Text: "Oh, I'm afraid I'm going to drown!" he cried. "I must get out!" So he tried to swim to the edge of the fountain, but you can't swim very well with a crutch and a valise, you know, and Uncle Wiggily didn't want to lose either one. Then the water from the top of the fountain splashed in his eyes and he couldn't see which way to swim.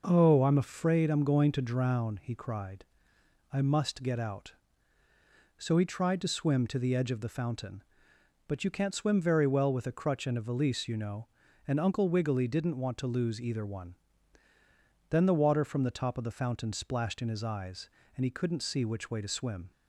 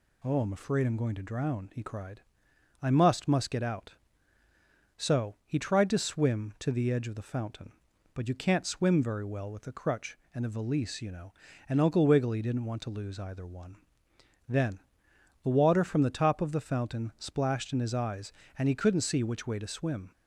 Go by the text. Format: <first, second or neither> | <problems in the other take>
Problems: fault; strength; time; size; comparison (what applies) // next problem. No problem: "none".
first | says "must" twice; at 3.2 s // pauses between "Then" and "the"; noticeable; at 14.8 s; 0.60 s long